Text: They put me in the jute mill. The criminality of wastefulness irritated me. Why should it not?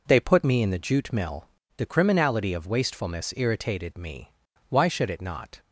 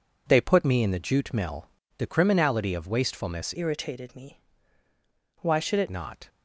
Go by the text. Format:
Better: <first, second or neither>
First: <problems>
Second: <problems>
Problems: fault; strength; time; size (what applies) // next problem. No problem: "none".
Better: first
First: none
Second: changes voice from "irritated" to "it"; from 3.5 to 5.8 s; 2.3 s long